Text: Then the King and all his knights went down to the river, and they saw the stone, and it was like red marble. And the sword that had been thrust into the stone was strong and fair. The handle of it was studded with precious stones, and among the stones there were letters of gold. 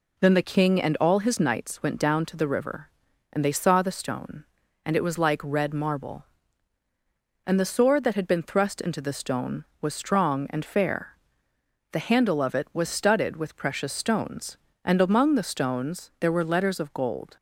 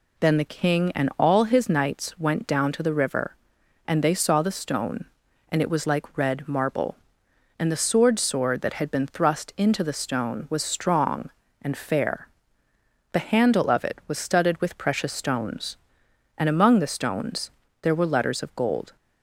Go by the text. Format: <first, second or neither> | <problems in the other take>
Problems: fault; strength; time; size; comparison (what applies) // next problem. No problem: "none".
first | says "sword" twice; at 8.1 s // pauses between "stones" and "there"; slight; at 17.4 s; 0.32 s long